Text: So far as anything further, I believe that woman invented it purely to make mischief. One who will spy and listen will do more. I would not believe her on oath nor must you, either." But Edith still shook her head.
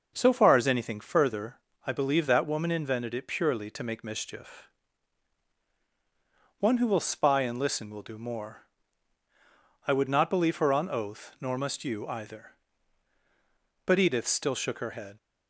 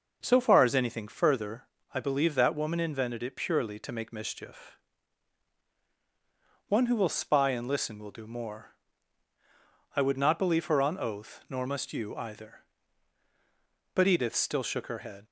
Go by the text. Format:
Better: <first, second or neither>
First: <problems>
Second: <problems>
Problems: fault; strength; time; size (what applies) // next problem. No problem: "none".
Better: neither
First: none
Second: none